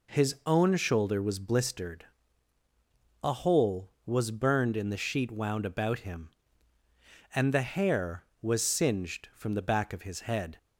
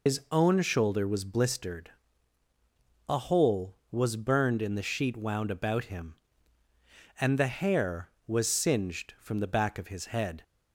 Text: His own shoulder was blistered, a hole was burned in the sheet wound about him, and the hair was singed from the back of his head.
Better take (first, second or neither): first